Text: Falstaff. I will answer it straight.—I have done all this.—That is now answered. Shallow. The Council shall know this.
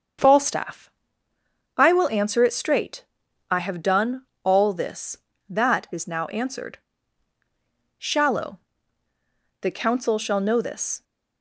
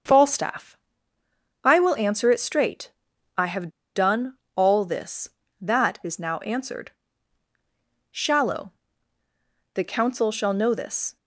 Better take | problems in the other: first | starts louder than the rest; until 1.9 s; 7 dB; also in the first // pauses between "have" and "done"; slight; at 3.6 s; 0.26 s long // pauses between "done" and "all"; slight; at 4.3 s; 0.20 s long; slight in the first // pauses between "now" and "answered"; slight; at 6.3 s; 0.16 s long

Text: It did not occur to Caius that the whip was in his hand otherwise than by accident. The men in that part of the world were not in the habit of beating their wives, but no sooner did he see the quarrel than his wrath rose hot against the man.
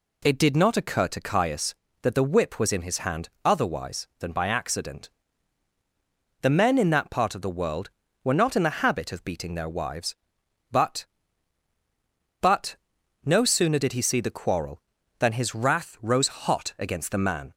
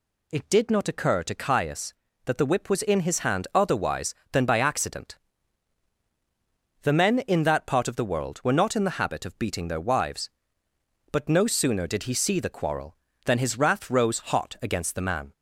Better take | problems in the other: second | pauses between "hand" and "otherwise"; slight; at 3.2 s; 0.16 s long // says "but" twice; at 12.3 s

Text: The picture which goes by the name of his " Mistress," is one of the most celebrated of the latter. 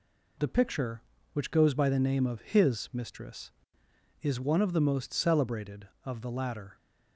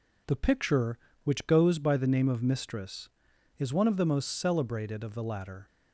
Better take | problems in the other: first | skips "his"; at 2.4 s

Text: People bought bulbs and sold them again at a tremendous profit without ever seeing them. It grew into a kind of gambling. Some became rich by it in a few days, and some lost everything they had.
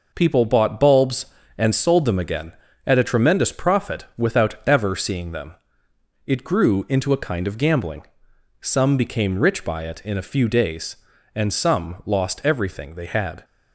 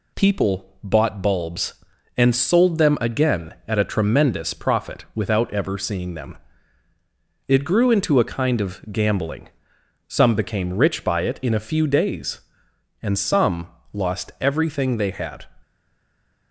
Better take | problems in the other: first | pauses between "some" and "lost"; slight; at 13.6 s; 0.24 s long // stays silent after the last word; slight; from 15.6 s on; 0.9 s long

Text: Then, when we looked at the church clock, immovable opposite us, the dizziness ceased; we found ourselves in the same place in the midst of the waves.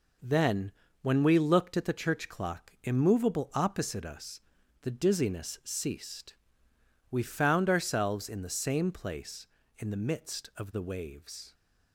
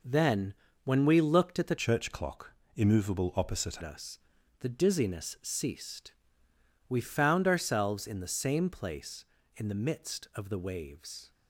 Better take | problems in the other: first | changes voice from "church" to "opposite"; from 1.7 to 3.8 s; 2.1 s long

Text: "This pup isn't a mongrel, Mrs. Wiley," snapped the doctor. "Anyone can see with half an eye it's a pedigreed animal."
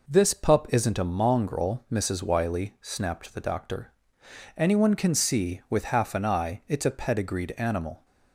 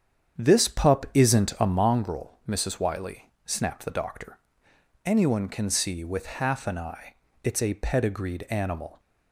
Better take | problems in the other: first | starts louder than the rest; strong; until 1.9 s; 8 dB // pauses between "eye" and "it's"; slight; at 7.1 s; 0.28 s long

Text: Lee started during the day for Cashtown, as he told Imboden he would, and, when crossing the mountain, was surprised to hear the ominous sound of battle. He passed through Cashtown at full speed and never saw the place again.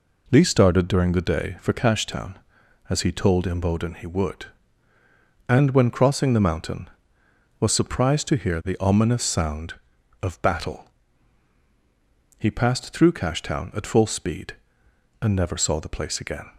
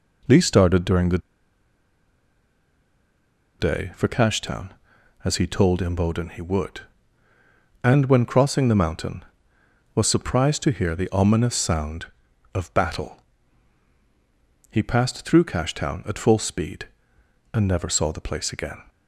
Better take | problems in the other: first | pauses between "the" and "day"; strong; at 1.1 s; 2.4 s long

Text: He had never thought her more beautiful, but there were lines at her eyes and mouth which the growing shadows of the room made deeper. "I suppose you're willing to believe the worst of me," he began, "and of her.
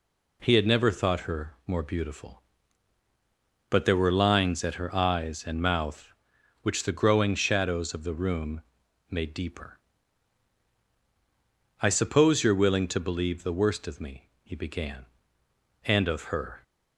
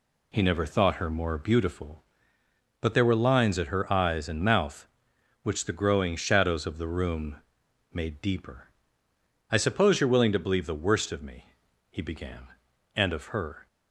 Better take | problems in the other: first | skips "had"; at 0.4 s // pauses between "room" and "made"; noticeable; at 7.3 s; 0.56 s long; noticeable in the first

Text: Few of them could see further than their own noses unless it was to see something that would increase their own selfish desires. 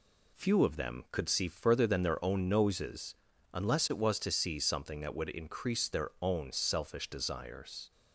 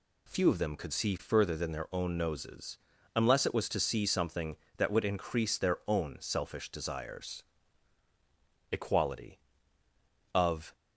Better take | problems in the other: first | pauses between "noses" and "unless"; at 2.7 s; 0.38 s long; slight in the first // goes on to say "Equality of"; strong; from 8.7 s on; 2.0 s long

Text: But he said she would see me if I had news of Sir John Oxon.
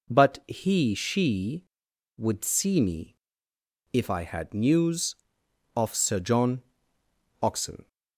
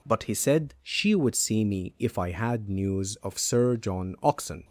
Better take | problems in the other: second | skips "said"; at 0.9 s // pauses between "me" and "if"; noticeable; at 3.1 s; 0.76 s long // pauses between "John" and "Oxon"; noticeable; at 6.6 s; 0.80 s long

